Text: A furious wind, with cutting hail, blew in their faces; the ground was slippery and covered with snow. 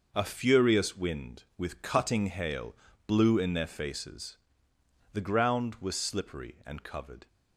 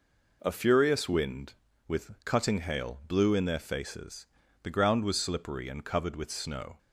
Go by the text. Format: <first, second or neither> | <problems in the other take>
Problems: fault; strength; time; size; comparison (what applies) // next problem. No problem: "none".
second | stops before "with snow"; at 7.2 s